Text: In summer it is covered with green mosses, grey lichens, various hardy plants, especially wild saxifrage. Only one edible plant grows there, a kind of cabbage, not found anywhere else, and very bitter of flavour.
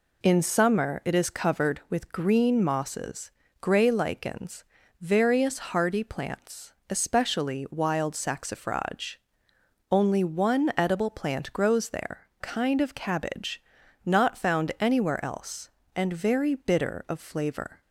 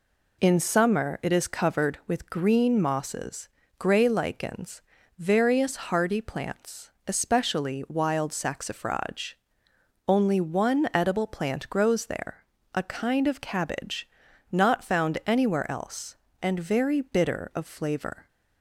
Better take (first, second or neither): second